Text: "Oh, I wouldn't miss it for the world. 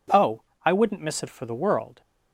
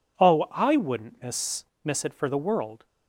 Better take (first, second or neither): first